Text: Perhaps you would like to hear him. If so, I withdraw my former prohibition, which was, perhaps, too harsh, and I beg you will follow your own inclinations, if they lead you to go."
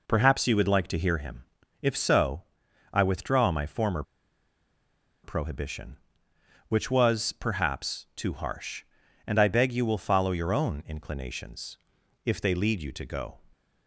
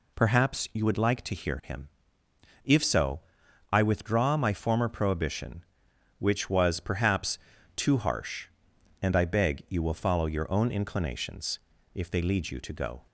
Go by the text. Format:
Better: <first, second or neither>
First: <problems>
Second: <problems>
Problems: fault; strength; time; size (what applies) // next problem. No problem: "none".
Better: second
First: pauses between "former" and "prohibition"; at 4.0 s; 1.2 s long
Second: none